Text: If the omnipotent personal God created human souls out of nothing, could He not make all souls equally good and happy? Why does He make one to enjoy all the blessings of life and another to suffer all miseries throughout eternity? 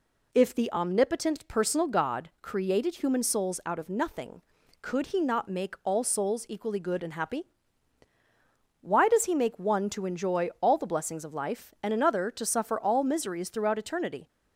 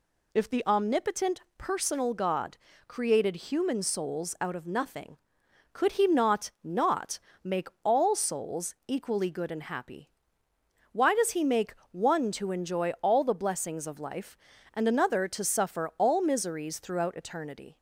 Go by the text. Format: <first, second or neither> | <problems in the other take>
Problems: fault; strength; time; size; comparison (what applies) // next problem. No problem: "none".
first | pauses between "omnipotent" and "personal"; slight; at 1.4 s; 0.16 s long // pauses between "God" and "created"; slight; at 2.5 s; 0.30 s long // says "not" twice; at 6.6 s // pauses between "make" and "all"; slight; at 7.6 s; 0.16 s long // pauses between "make" and "one"; slight; at 11.7 s; 0.18 s long